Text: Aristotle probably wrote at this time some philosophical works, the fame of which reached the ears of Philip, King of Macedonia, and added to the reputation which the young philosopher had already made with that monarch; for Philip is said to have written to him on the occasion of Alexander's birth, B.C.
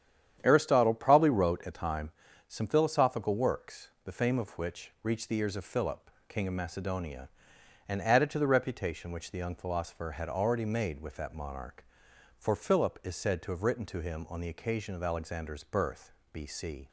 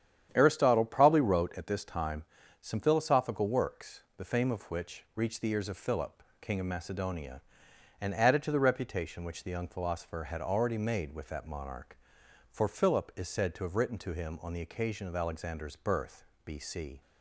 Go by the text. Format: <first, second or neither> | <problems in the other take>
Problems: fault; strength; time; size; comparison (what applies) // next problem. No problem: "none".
second | starts louder than the rest; strong; until 1.4 s; 9.5 dB; strong in the second // skips "this"; at 1.7 s // pauses between "time" and "some"; at 2.0 s; 0.38 s long; also in the second